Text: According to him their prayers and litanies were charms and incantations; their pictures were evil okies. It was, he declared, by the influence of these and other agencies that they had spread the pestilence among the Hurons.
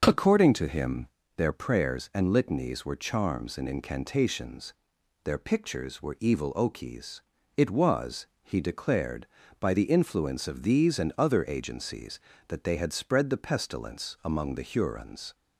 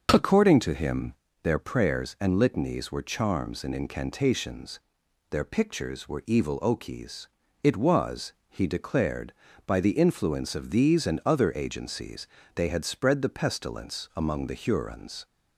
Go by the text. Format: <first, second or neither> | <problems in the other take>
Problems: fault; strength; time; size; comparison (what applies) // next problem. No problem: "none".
first | starts louder than the rest; until 1.1 s; 6 dB; noticeable in the first // pauses between "him" and "their"; slight; at 1.1 s; 0.30 s long; slight in the first // skips "that"; at 12.4 s